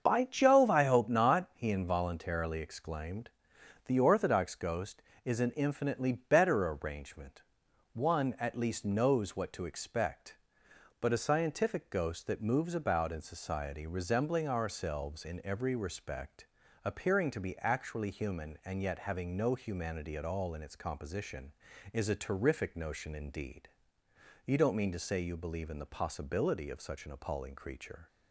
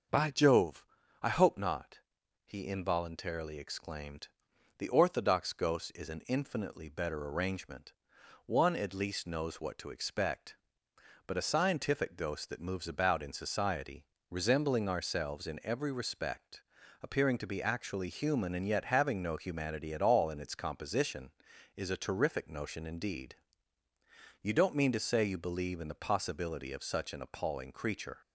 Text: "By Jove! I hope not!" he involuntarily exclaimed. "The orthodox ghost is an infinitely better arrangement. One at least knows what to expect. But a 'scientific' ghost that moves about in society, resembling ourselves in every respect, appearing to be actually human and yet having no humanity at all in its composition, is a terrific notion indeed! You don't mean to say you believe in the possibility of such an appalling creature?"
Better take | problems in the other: neither | starts louder than the rest; the same in both

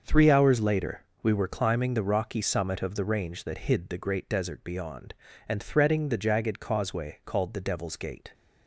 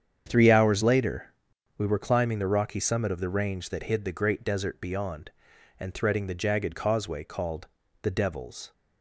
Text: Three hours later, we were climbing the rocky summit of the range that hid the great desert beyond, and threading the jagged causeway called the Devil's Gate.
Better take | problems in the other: first | starts louder than the rest; strong; until 1.2 s; 8 dB; also in the first // pauses between "called" and "the"; slight; at 7.6 s; 0.34 s long // stops before "Gate"; at 8.7 s

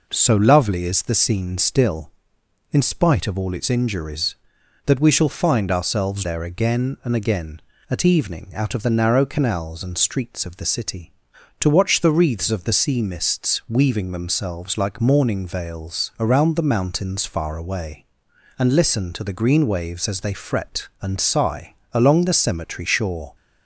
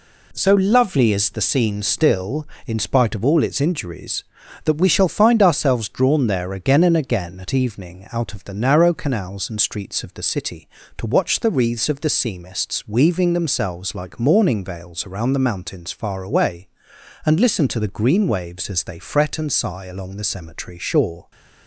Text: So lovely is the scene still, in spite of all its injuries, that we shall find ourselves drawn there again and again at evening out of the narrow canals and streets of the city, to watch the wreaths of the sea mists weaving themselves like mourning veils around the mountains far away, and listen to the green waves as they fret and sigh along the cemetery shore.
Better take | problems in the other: second | skips "drawn"; at 6.2 s // pauses between "sigh" and "along"; slight; at 21.7 s; 0.18 s long

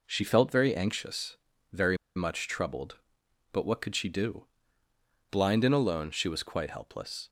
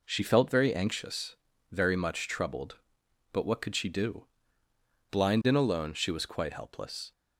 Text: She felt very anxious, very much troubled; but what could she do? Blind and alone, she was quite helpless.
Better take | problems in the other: second | pauses between "very" and "much"; slight; at 1.9 s; 0.20 s long

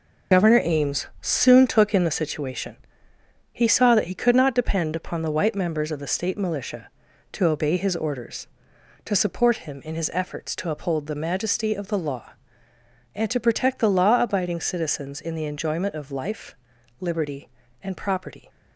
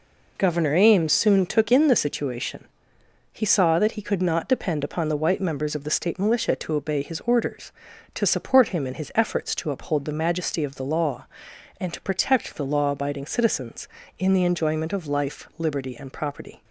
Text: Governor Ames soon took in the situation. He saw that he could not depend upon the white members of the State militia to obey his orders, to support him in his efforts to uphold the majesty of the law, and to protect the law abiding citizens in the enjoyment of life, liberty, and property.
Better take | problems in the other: second | loses the start of "Governor"; at 0.3 s; 100 ms

